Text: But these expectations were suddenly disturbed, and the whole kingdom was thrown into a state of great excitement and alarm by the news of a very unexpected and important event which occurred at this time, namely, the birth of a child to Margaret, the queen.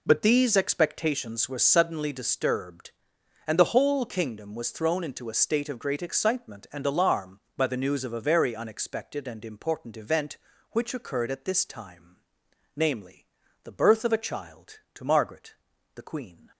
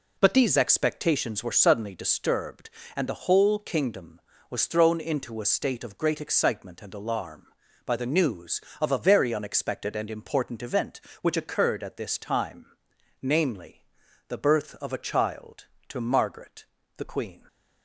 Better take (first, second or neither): neither